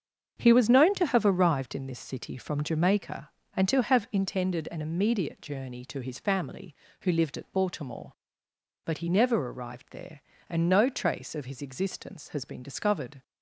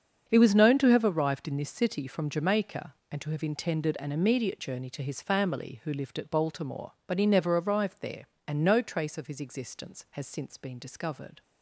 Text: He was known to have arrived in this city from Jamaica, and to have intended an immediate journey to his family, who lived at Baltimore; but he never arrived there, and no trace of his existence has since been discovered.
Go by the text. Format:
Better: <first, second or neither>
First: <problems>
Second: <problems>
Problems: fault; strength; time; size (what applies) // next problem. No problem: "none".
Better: second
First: starts louder than the rest; strong; until 1.3 s; 7 dB // skips "since"; at 12.4 s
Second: starts louder than the rest; until 1.3 s; 7 dB